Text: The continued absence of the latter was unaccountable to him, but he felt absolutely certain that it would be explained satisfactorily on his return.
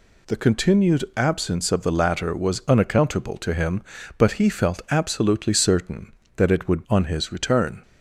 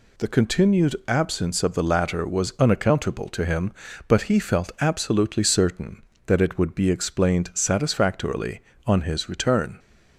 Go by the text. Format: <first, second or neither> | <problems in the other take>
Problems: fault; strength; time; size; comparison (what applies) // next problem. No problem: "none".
second | skips "be explained satisfactorily"; at 6.8 s